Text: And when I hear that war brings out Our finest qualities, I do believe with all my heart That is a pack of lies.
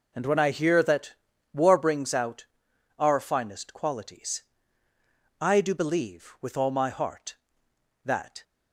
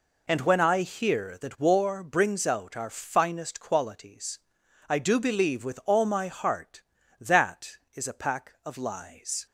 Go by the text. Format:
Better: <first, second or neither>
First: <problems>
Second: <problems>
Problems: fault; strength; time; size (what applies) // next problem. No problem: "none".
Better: second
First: pauses between "that" and "war"; at 1.1 s; 0.40 s long // pauses between "out" and "Our"; noticeable; at 2.4 s; 0.54 s long // stops before "is a pack of lies"; at 8.4 s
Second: none